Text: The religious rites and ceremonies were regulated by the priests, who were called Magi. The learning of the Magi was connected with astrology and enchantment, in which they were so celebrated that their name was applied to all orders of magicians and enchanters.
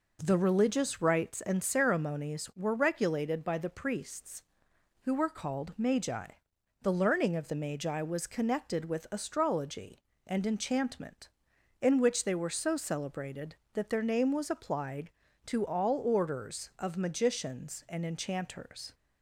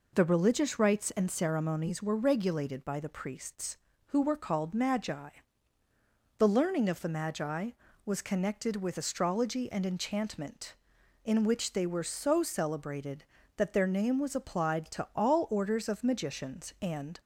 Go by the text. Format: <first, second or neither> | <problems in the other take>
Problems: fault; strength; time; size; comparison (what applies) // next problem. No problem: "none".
first | stops before "enchanters"; at 17.2 s